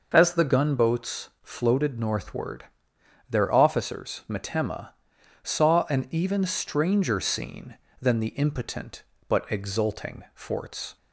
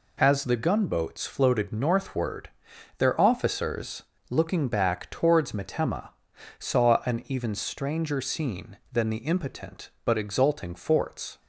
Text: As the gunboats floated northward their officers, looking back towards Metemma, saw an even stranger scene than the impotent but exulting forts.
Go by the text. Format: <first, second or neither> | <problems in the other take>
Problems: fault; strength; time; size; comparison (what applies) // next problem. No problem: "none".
second | pauses between "northward" and "their"; noticeable; at 2.6 s; 0.66 s long; noticeable in the second // skips "looking back towards"; at 4.2 s